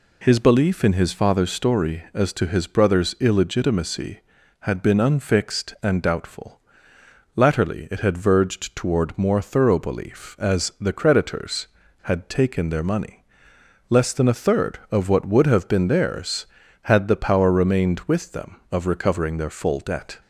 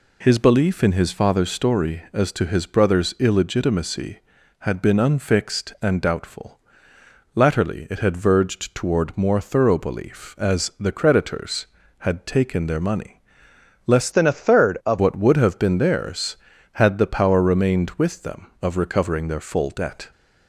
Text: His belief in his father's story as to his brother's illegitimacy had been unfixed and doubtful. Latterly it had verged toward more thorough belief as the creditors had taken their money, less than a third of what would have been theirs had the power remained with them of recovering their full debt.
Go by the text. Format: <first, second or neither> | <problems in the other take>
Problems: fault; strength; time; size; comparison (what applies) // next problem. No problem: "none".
first | changes voice from "than" to "of"; from 14.1 to 14.9 s; 0.8 s long